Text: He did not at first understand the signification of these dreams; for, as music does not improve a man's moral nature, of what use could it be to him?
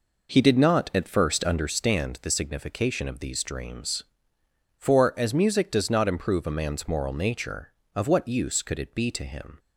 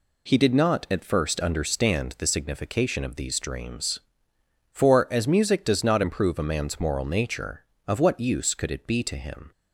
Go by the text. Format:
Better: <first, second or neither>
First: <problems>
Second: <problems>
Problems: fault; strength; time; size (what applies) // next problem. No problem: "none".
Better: second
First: starts louder than the rest; noticeable; until 1.6 s; 5 dB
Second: none